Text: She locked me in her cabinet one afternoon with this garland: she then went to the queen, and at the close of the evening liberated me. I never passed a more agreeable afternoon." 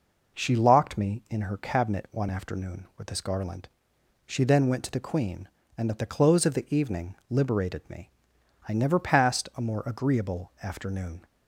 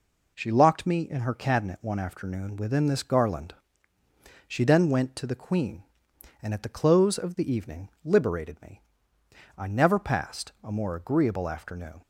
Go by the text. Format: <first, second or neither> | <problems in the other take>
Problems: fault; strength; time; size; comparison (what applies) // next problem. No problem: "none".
first | says "within" for "with"; at 2.5 s